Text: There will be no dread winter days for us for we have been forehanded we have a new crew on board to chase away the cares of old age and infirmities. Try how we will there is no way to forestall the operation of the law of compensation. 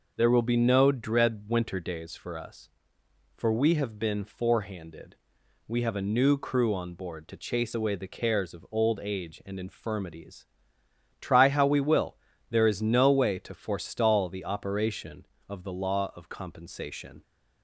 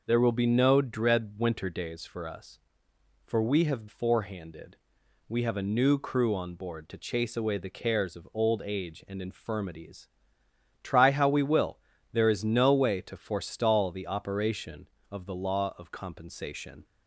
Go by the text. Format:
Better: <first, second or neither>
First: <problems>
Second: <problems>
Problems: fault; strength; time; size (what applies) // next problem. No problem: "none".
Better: first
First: pauses between "forehanded" and "we"; noticeable; at 5.1 s; 0.50 s long // pauses between "will" and "there"; slight; at 12.1 s; 0.34 s long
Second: skips "been"; at 3.8 s // pauses between "forehanded" and "we"; noticeable; at 4.7 s; 0.50 s long // pauses between "will" and "there"; slight; at 11.7 s; 0.34 s long